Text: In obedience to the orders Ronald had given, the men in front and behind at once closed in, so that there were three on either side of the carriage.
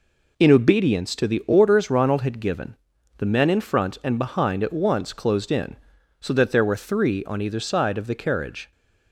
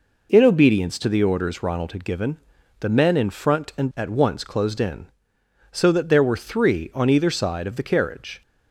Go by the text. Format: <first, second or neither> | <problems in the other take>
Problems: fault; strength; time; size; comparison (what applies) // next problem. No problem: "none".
first | skips "behind"; at 3.9 s